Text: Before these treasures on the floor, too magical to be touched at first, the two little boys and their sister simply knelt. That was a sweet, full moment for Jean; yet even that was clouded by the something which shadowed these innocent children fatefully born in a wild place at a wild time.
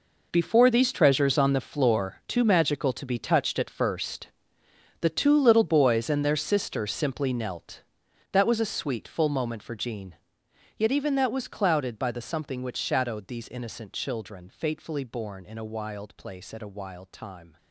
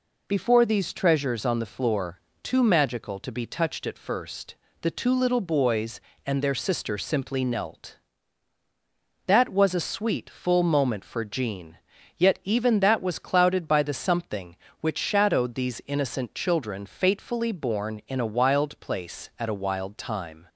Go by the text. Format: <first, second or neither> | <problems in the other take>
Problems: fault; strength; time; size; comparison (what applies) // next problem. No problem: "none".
second | gets quieter; strong; throughout; 14 dB